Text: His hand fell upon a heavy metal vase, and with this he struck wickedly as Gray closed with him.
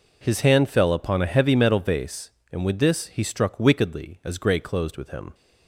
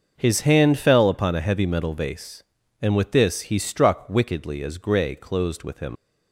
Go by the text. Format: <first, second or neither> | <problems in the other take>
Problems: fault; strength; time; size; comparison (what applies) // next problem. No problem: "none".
first | starts louder than the rest; until 1.1 s; 6 dB // leaves "him" unfinished; at 5.9 s; 50 ms